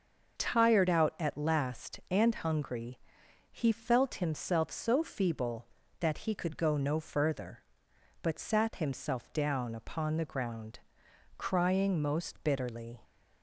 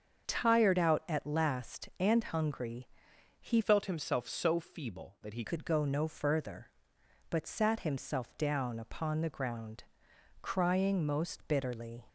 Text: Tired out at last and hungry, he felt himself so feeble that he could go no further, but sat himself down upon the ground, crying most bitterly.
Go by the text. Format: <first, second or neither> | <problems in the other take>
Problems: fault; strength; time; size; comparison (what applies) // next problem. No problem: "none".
first | starts louder than the rest; until 1.3 s; 6.5 dB; also in the first // changes voice from "felt" to "he"; from 3.6 to 5.4 s; 1.8 s long